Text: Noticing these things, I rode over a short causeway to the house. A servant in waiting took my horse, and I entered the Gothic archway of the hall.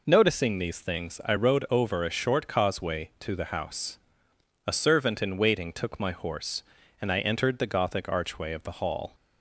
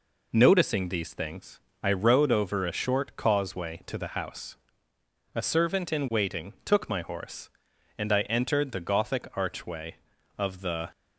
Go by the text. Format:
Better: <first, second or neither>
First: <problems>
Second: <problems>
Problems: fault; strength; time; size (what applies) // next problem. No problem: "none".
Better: first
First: none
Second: stops before "hall"; at 10.9 s